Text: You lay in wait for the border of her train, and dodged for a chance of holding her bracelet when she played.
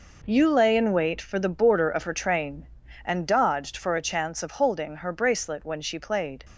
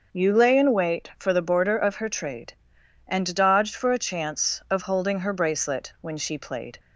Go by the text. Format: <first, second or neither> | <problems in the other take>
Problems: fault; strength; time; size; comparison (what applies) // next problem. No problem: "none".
first | says "trade" for "train"; at 2.0 s